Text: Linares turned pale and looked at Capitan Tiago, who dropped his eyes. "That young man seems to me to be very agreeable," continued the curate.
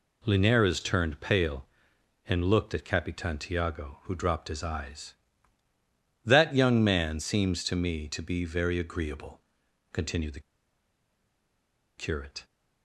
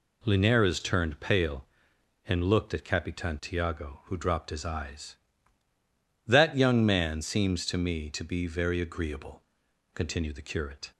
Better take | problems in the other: second | pauses between "the" and "curate"; strong; at 10.3 s; 1.5 s long

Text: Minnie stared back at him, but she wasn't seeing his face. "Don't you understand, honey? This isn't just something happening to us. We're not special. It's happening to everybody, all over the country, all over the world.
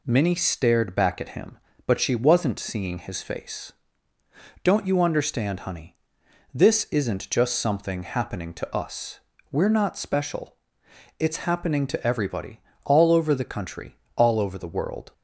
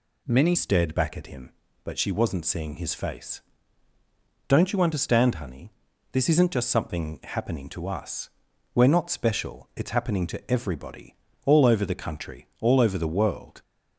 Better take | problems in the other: first | changes voice at "stared"; from 0.5 s on; 13.1 s long

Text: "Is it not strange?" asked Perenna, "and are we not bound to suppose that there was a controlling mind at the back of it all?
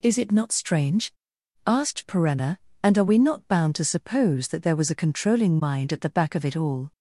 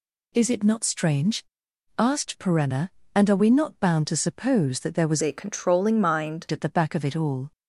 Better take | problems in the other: first | changes voice from "a" to "mind"; from 5.2 to 6.4 s; 1.2 s long

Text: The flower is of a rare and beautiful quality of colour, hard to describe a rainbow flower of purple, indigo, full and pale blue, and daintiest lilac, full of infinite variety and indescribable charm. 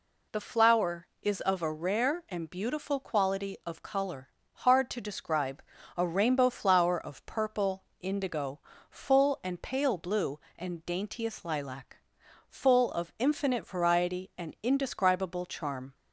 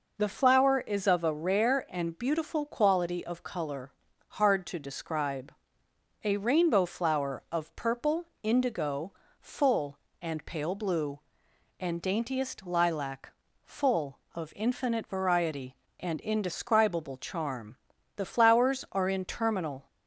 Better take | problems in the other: first | pauses between "describe" and "a"; noticeable; at 5.5 s; 0.70 s long; slight in the first // goes on to say "The flowers are in terminal"; strong; from 18.1 s on; 1.7 s long

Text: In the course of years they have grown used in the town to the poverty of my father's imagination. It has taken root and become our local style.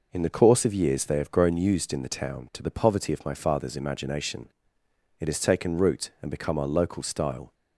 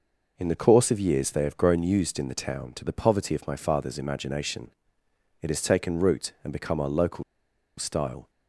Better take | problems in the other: first | pauses between "local" and "style"; noticeable; at 7.2 s; 0.54 s long

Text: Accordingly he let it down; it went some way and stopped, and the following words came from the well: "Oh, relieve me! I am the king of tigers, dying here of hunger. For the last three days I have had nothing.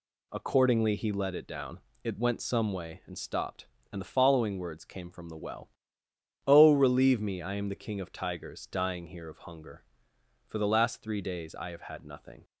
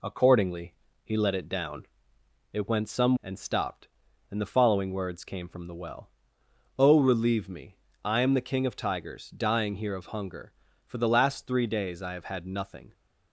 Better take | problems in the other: first | pauses between "Accordingly" and "he"; slight; at 0.7 s; 0.28 s long // skips "way"; at 3.2 s

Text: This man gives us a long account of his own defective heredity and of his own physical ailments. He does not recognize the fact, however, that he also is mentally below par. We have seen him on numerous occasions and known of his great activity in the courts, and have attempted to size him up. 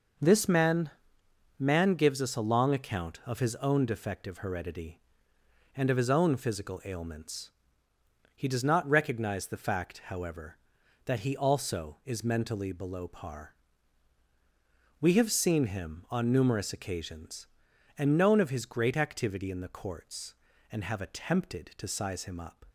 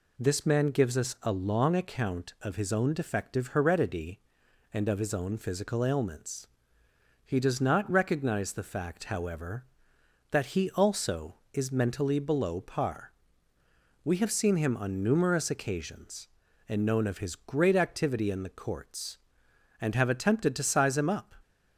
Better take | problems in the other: second | says "man" twice; at 1.5 s

